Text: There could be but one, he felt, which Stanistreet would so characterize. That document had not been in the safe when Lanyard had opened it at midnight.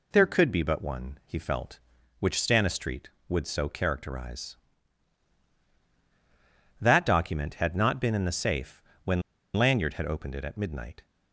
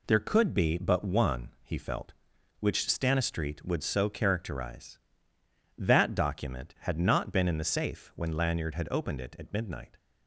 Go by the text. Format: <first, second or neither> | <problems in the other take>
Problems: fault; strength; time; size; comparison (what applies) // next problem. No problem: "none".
second | pauses between "safe" and "when"; slight; at 8.8 s; 0.24 s long // pauses between "when" and "Lanyard"; slight; at 9.2 s; 0.34 s long